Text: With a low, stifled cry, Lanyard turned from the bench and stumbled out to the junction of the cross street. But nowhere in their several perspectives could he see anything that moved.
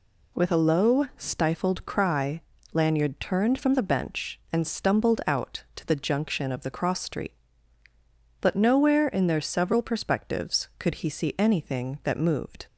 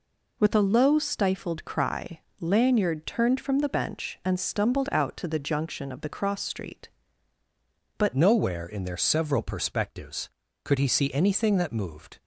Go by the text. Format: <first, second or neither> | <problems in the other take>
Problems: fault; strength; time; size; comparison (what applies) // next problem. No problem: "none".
first | changes voice at "nowhere"; from 8.1 s on; 4.0 s long